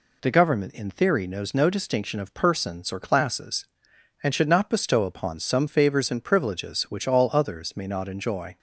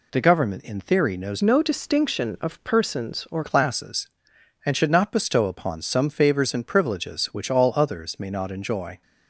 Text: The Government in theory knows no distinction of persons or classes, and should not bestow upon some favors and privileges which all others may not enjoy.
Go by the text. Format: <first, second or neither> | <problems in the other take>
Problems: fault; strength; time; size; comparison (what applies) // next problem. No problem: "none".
first | changes voice from "no" to "or"; from 1.4 to 3.4 s; 2.0 s long